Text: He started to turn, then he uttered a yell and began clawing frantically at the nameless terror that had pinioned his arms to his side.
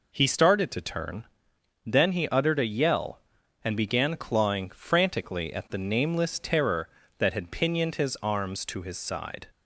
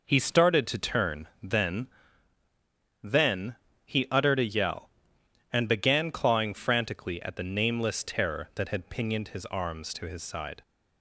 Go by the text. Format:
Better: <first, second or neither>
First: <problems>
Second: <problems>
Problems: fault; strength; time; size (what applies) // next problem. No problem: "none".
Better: first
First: none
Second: says "then" twice; at 3.0 s